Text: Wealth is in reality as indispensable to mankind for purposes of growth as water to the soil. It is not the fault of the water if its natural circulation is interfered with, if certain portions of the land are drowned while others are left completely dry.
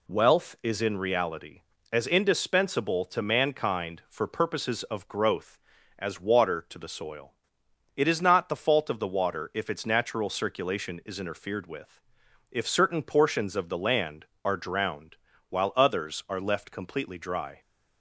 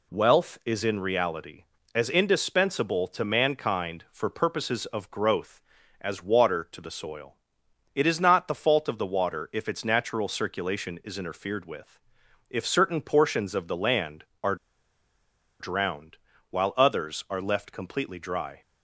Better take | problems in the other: first | pauses between "are" and "drowned"; at 14.5 s; 1.0 s long // pauses between "drowned" and "while"; slight; at 16.1 s; 0.34 s long; slight in the first

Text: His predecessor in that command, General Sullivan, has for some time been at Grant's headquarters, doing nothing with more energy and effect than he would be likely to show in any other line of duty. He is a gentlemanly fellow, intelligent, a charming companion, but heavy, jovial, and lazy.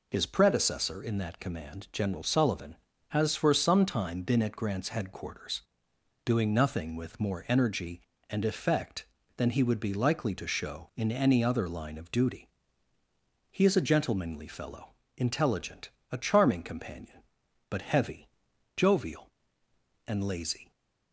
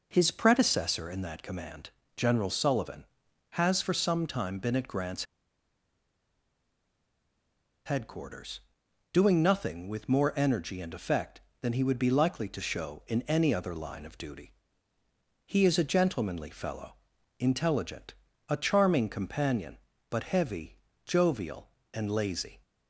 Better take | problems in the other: first | pauses between "Grant's" and "headquarters"; strong; at 5.2 s; 2.6 s long

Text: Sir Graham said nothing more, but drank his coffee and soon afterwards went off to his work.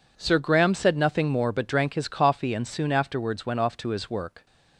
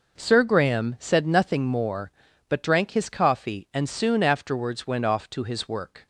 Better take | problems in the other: neither | none

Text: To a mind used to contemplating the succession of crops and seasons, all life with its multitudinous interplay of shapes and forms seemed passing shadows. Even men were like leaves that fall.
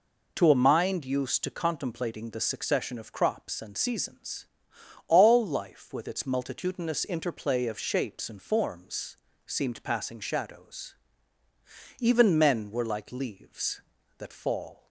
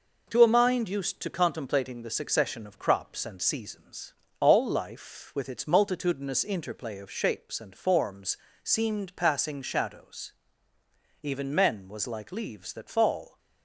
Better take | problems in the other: first | pauses between "forms" and "seemed"; slight; at 8.3 s; 0.28 s long; slight in the first // says "was" for "were"; at 11.8 s

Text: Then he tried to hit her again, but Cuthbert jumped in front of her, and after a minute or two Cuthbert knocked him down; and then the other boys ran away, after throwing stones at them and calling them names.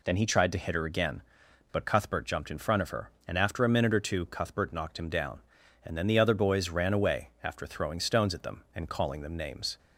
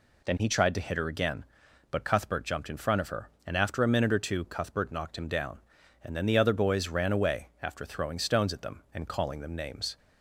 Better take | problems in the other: neither | none

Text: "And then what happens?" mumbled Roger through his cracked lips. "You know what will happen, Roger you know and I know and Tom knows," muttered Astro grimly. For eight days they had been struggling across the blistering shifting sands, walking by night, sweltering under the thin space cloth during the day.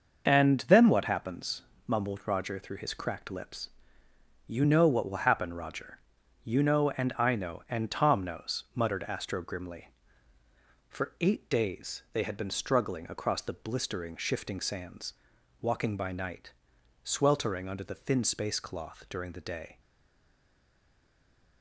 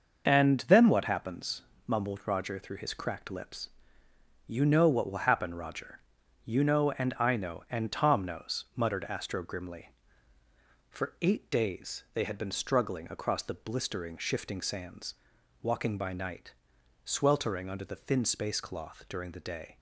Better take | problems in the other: second | starts louder than the rest; noticeable; until 1.2 s; 6 dB; noticeable in the second // pauses between "Roger" and "you"; noticeable; at 5.9 s; 0.48 s long; noticeable in the second // stays silent after the last word; noticeable; from 19.7 s on; 1.9 s long

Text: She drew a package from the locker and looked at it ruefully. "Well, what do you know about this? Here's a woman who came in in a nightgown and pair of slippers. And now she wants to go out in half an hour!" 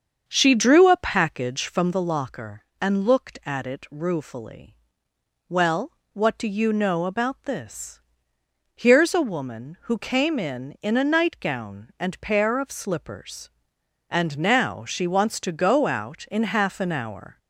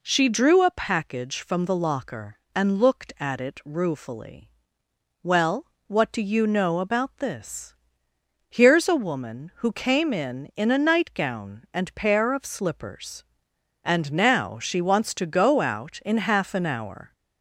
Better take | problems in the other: second | starts louder than the rest; until 1.9 s; 7 dB

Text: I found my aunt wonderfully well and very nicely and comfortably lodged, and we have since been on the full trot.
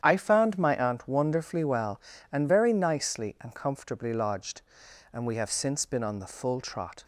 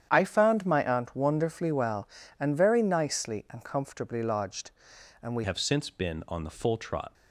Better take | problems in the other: first | starts louder than the rest; strong; until 1.1 s; 9 dB; strong in the first // changes voice at "have"; from 5.4 s on; 1.7 s long

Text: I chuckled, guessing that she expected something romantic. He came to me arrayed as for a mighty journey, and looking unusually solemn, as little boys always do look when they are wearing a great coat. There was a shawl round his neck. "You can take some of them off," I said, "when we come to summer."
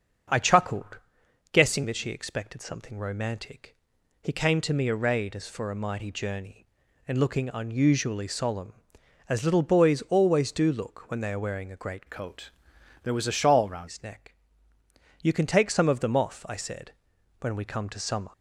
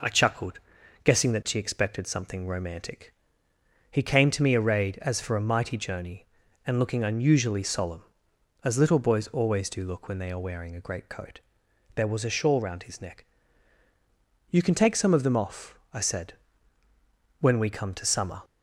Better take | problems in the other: second | starts louder than the rest; until 1.8 s; 6.5 dB // changes voice from "coat" to "round"; from 12.0 to 13.8 s; 1.8 s long

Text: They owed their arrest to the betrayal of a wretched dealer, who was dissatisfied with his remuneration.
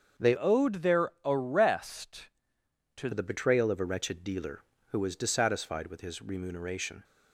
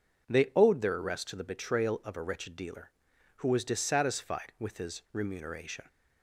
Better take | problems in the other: second | starts louder than the rest; until 1.3 s; 7 dB // changes voice from "owed" to "to"; from 0.3 to 3.1 s; 2.8 s long

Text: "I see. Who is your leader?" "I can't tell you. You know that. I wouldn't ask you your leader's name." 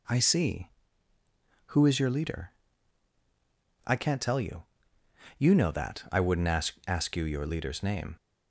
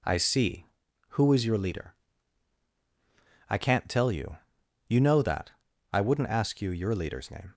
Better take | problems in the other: second | says "ask" twice; at 6.8 s

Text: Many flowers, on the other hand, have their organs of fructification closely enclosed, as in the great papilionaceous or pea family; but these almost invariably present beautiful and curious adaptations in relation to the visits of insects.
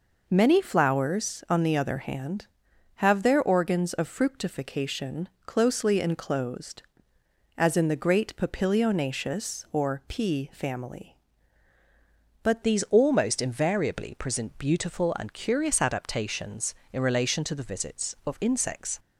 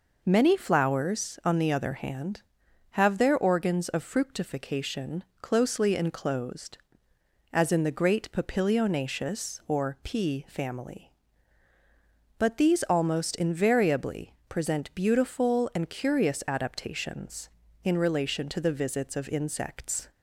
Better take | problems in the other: second | pauses between "fructification" and "closely"; slight; at 5.2 s; 0.16 s long; slight in the second // changes voice at "these"; from 12.6 s on; 6.3 s long

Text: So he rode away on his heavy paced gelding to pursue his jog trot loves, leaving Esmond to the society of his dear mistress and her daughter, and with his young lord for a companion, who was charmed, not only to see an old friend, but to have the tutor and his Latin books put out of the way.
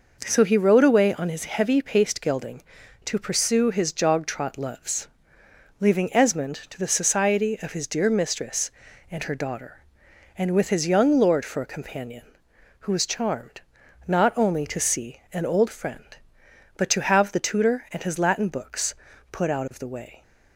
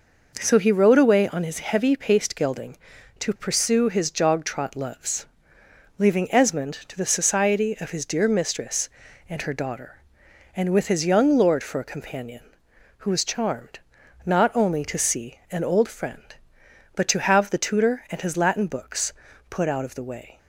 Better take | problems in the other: neither | pauses between "books" and "put"; the same in both

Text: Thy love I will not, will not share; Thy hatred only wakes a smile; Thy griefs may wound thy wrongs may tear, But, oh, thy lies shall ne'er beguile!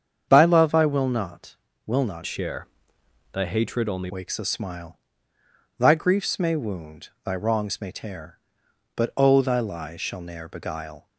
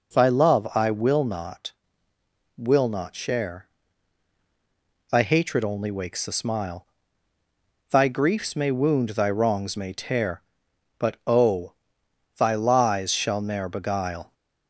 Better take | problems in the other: second | starts louder than the rest; strong; until 1.3 s; 7.5 dB // changes voice from "share" to "only"; from 2.2 to 4.0 s; 1.8 s long // pauses between "wound" and "thy"; slight; at 7.0 s; 0.16 s long

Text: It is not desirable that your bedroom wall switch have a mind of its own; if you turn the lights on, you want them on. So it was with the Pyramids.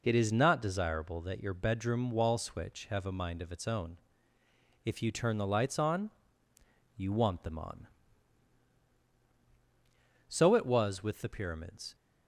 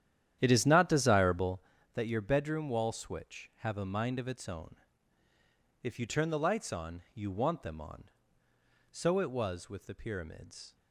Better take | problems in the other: first | starts louder than the rest; strong; until 1.7 s; 10.5 dB

